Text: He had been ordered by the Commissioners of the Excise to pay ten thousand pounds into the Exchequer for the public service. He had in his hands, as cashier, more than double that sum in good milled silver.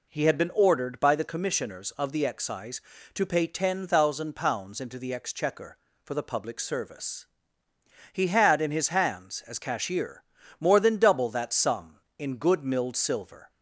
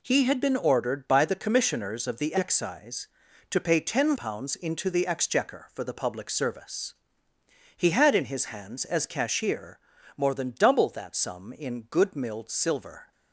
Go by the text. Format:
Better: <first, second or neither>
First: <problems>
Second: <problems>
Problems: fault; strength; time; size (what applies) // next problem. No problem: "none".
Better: first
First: none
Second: skips "thousand"; at 4.1 s